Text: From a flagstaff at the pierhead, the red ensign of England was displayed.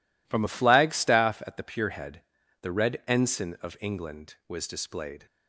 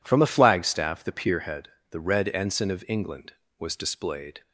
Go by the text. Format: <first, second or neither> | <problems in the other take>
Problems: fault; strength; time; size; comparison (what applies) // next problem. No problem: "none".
first | skips "at"; at 1.0 s